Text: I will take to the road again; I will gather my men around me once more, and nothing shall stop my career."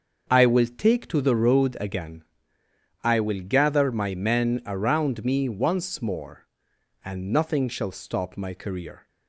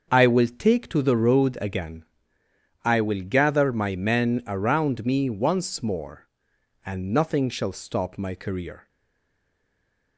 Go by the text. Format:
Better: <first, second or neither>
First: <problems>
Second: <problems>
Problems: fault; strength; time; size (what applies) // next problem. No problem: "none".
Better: first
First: starts louder than the rest; until 1.2 s; 6.5 dB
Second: starts louder than the rest; until 1.1 s; 6.5 dB // stays silent after the last word; noticeable; from 8.8 s on; 1.3 s long